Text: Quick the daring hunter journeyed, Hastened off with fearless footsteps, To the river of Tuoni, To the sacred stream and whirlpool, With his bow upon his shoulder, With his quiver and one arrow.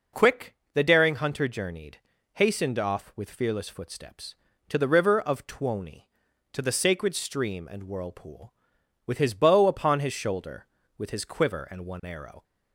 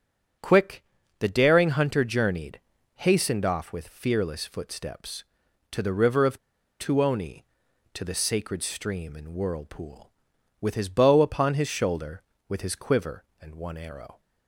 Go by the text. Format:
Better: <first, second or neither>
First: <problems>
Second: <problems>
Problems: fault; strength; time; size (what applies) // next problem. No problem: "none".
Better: first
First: pauses between "Quick" and "the"; slight; at 0.5 s; 0.20 s long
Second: starts louder than the rest; until 1.7 s; 7 dB // pauses between "Quick" and "the"; slight; at 0.8 s; 0.36 s long // pauses between "of" and "Tuoni"; at 6.3 s; 0.42 s long